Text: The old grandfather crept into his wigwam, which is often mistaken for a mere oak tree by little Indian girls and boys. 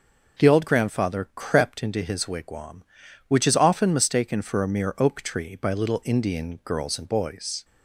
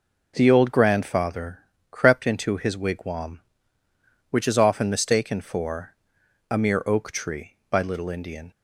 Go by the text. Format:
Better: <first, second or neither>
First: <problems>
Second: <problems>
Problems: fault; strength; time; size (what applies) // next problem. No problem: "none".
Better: first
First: none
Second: pauses between "grandfather" and "crept"; slight; at 1.6 s; 0.32 s long // pauses between "for" and "a"; noticeable; at 5.9 s; 0.56 s long // stops before "girls and boys"; at 8.5 s